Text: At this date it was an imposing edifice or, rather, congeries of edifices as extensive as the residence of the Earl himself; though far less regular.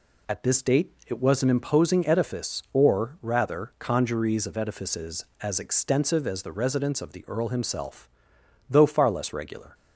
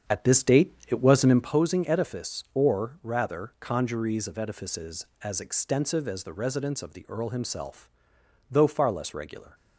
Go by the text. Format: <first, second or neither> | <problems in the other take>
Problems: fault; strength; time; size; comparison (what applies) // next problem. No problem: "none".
first | starts louder than the rest; strong; until 1.6 s; 7.5 dB // pauses between "date" and "it"; slight; at 0.7 s; 0.16 s long; slight in the first